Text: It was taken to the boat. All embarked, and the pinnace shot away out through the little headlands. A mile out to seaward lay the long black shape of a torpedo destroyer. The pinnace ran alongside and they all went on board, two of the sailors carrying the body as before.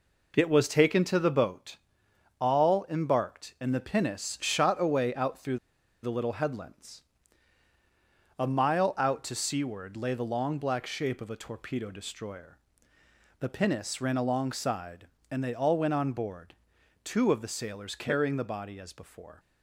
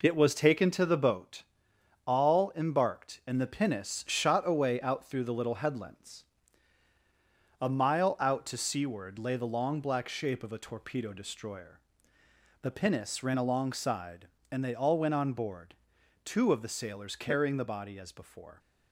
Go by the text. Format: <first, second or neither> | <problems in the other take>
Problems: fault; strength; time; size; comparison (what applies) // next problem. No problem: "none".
second | pauses between "through" and "the"; at 5.5 s; 0.45 s long